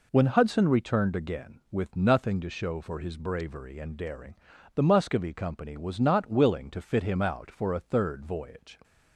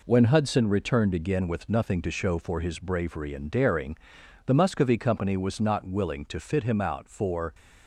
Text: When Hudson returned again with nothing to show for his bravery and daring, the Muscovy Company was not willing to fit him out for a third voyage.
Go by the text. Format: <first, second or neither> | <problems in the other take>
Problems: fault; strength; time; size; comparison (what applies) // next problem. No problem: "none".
first | stops before "a third voyage"; at 7.5 s